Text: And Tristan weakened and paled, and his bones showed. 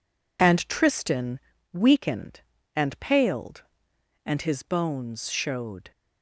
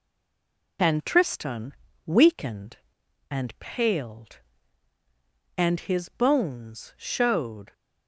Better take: first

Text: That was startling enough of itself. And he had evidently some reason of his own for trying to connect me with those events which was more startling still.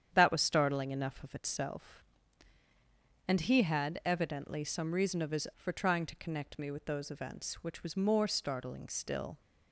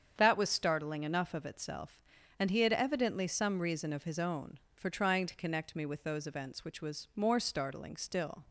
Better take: second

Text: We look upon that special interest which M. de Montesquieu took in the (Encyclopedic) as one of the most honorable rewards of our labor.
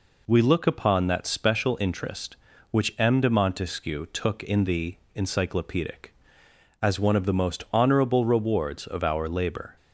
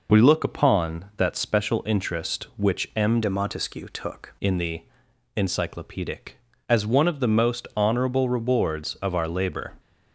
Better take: first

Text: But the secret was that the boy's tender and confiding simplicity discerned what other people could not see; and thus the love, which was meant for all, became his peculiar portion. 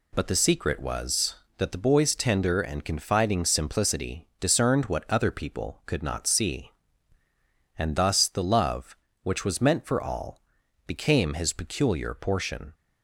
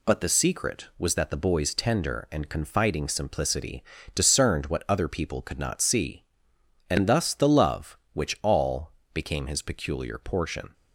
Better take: first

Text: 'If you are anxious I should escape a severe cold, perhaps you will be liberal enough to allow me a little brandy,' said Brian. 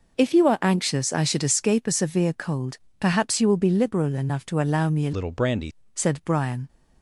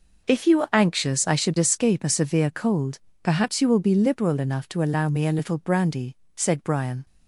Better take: second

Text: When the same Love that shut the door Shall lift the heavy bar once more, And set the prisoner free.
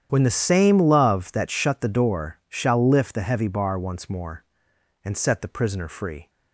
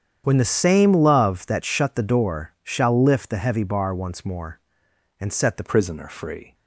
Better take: first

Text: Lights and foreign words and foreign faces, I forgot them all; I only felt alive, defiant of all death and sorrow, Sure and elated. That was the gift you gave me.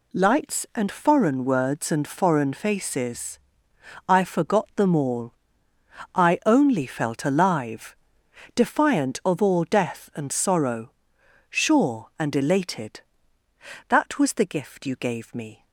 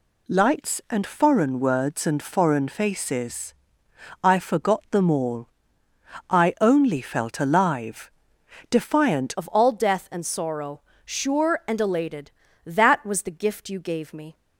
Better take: first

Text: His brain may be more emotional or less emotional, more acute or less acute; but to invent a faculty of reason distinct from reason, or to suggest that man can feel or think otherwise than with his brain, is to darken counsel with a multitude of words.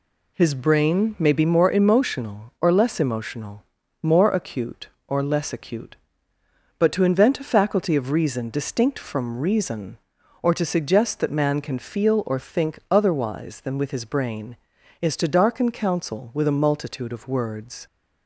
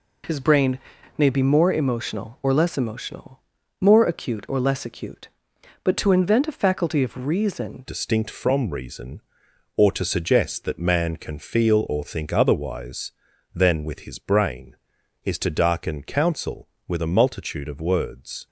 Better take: first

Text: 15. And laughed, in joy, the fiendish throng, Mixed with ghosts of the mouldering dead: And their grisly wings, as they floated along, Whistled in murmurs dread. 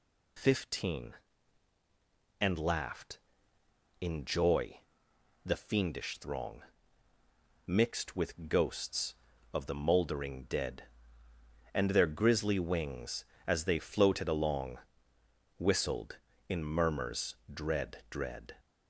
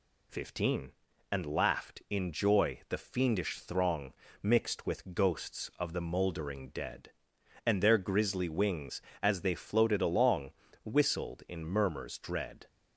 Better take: second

